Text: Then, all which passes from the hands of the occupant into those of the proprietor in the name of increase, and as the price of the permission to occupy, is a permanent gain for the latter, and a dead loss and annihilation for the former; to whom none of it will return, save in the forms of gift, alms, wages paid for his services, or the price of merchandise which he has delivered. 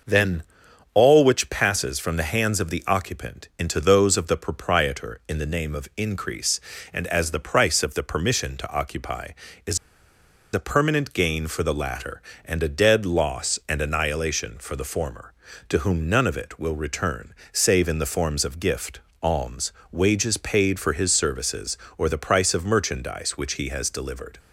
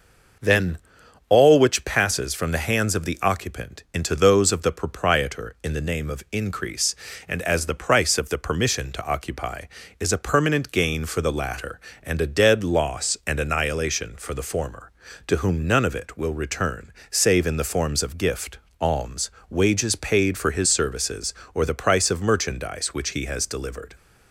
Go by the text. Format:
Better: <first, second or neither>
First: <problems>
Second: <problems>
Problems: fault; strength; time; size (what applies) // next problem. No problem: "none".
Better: second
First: pauses between "is" and "a"; noticeable; at 9.7 s; 0.76 s long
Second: none